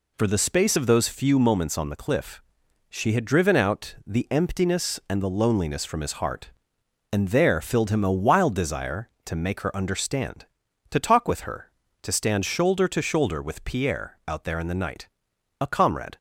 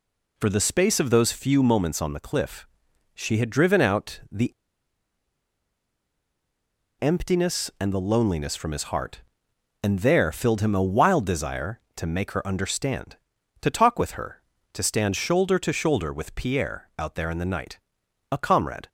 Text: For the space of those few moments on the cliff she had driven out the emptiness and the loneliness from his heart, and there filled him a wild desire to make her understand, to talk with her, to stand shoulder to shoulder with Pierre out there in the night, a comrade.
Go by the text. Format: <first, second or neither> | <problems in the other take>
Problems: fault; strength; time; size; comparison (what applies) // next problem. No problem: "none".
first | pauses between "cliff" and "she"; noticeable; at 2.6 s; 0.48 s long; noticeable in the first // pauses between "the" and "emptiness"; strong; at 4.5 s; 2.4 s long